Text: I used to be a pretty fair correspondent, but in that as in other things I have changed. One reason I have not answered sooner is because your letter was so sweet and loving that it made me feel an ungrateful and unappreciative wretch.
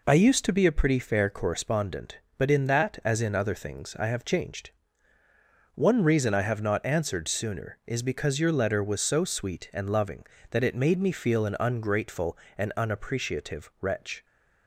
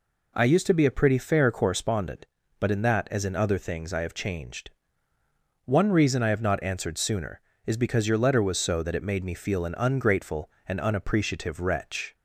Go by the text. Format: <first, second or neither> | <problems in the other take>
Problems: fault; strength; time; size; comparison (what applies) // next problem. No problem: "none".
first | skips "sweet and loving"; at 8.8 s